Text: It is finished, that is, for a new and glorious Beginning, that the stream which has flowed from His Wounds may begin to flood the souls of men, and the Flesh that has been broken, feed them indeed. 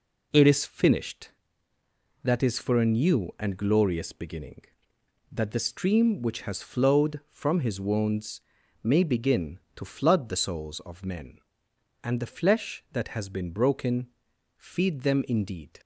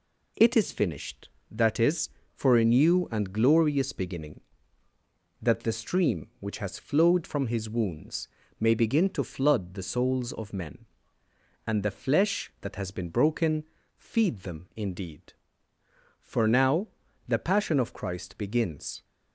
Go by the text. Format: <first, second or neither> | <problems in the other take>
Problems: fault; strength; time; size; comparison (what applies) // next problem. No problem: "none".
first | pauses between "Wounds" and "may"; slight; at 8.2 s; 0.32 s long; also in the first // goes on to say "For now the Passion of Christ begins"; strong; from 16.2 s on; 2.8 s long